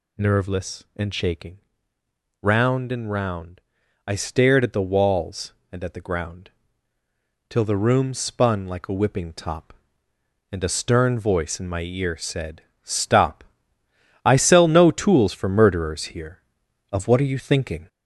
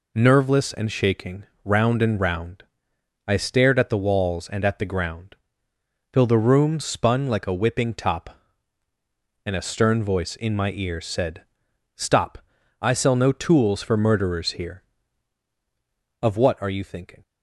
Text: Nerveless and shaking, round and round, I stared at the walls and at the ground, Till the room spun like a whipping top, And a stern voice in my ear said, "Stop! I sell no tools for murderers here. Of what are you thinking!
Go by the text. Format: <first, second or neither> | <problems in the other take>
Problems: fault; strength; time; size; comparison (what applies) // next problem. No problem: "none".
second | gets louder; noticeable; throughout; 4.5 dB